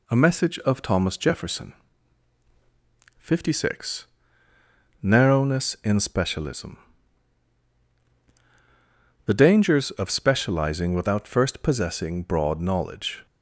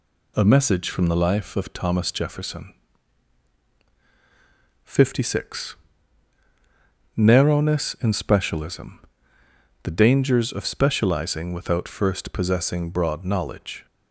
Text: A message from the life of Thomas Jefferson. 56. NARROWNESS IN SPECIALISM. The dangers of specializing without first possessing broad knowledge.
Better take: second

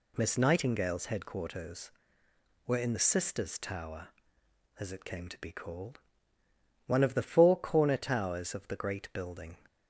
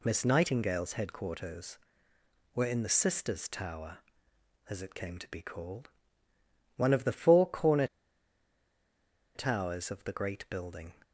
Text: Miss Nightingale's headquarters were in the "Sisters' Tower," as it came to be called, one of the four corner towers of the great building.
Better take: first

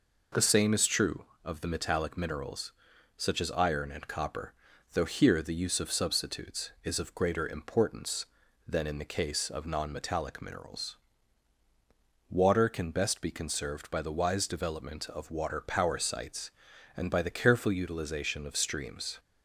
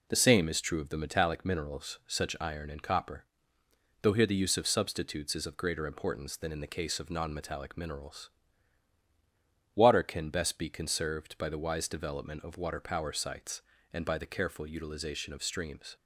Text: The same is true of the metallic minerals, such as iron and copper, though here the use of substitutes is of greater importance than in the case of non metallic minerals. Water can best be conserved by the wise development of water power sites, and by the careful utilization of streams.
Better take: first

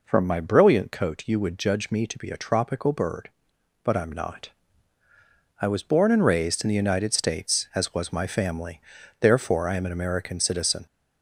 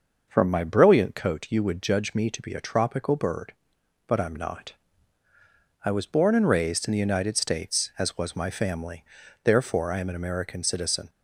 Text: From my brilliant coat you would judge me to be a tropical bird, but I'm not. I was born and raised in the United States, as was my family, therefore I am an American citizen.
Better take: second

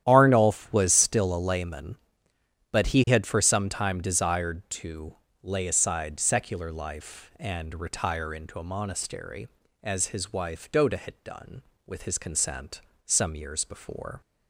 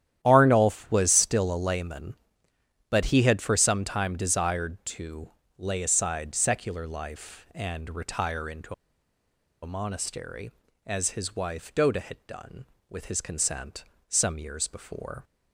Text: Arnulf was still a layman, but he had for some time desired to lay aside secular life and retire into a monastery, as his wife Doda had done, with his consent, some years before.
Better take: first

